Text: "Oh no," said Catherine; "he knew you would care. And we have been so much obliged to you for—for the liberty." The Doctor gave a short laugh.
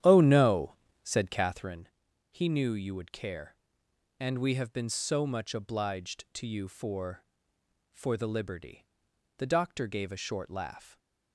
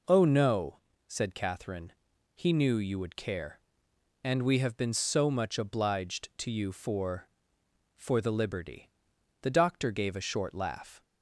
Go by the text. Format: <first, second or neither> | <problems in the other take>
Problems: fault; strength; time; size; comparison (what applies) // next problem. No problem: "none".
second | starts louder than the rest; strong; until 1.8 s; 10.5 dB